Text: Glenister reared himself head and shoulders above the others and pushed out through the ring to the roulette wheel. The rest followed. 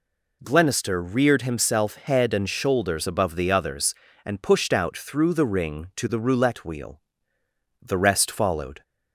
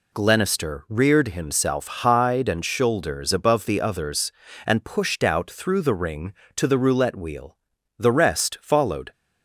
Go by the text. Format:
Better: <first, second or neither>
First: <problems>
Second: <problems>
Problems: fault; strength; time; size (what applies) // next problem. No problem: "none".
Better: first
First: none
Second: says "hide" for "head"; at 1.8 s